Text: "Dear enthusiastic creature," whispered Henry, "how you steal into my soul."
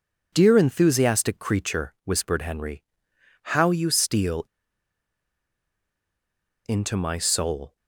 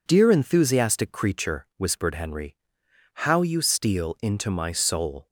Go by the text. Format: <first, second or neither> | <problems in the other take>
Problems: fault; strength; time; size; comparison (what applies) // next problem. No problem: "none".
second | pauses between "steal" and "into"; strong; at 4.4 s; 2.1 s long